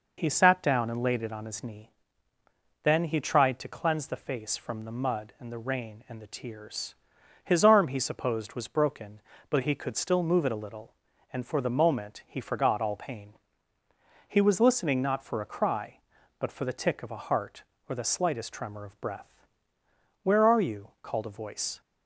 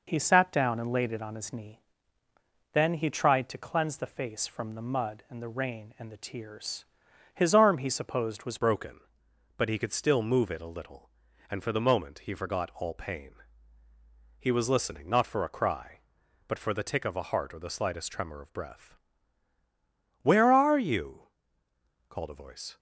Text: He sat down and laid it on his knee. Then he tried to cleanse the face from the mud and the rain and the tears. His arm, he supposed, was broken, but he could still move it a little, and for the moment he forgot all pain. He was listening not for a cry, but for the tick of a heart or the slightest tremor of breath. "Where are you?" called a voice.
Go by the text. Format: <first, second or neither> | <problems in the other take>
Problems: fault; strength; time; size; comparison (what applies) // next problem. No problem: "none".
first | changes voice at "broken"; from 8.5 s on; 14.2 s long